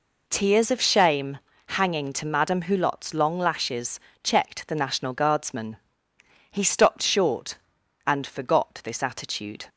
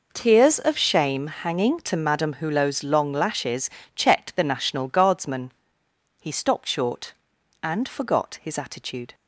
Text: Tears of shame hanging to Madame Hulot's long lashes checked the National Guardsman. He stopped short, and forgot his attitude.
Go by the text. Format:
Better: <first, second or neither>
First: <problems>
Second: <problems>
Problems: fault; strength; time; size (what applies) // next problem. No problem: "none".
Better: second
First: pauses between "shame" and "hanging"; slight; at 1.3 s; 0.30 s long // pauses between "lashes" and "checked"; slight; at 4.0 s; 0.24 s long // says "this" for "his"; at 8.8 s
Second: pauses between "lashes" and "checked"; slight; at 3.7 s; 0.24 s long